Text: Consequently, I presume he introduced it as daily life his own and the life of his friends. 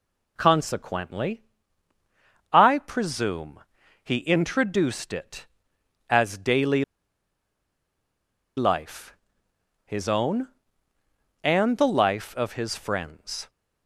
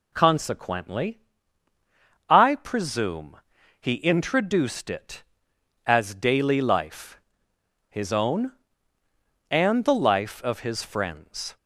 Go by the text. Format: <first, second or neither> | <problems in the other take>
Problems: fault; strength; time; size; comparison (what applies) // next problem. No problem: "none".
second | pauses between "presume" and "he"; at 3.6 s; 0.42 s long; also in the second // pauses between "daily" and "life"; strong; at 6.8 s; 1.7 s long // pauses between "life" and "his"; noticeable; at 9.1 s; 0.70 s long; noticeable in the second